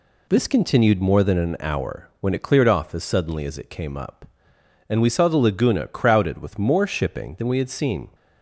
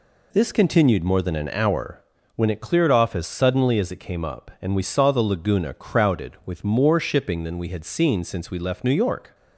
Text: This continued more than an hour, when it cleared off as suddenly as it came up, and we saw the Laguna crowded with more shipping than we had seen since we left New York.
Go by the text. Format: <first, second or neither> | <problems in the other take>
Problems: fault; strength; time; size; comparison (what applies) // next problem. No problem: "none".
second | stops before "since we left New York"; at 8.1 s